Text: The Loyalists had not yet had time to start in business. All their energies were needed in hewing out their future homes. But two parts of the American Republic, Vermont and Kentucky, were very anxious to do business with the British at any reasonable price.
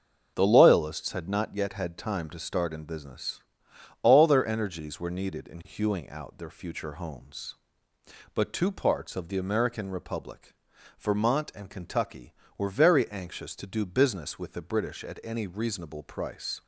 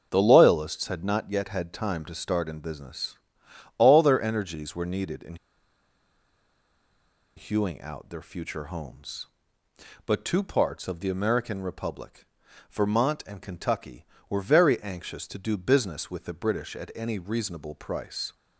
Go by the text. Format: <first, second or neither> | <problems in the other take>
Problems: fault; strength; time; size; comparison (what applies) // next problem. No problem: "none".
first | starts louder than the rest; until 1.1 s; 6.5 dB; also in the first // pauses between "in" and "hewing"; strong; at 5.3 s; 2.0 s long